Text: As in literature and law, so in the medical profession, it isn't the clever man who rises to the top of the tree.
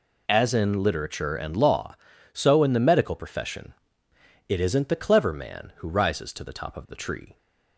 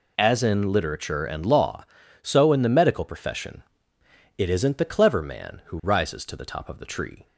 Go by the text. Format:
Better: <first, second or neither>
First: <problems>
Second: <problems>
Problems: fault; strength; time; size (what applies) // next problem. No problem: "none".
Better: neither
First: none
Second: none